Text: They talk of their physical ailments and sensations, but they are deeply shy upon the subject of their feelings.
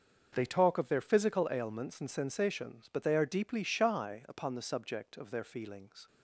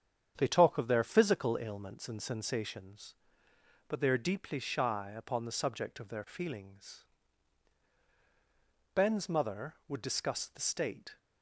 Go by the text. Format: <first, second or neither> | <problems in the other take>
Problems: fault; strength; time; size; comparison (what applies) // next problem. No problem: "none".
first | starts louder than the rest; strong; until 1.3 s; 8.5 dB; also in the first // goes on to say "Ben's mother would discuss the state"; strong; from 8.9 s on; 2.2 s long